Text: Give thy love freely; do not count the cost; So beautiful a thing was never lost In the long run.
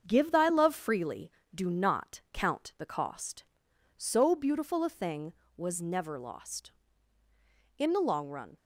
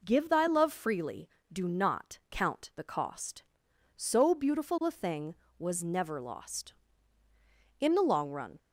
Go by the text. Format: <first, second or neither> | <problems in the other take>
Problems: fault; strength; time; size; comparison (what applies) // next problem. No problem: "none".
second | gets quieter; noticeable; throughout; 4.5 dB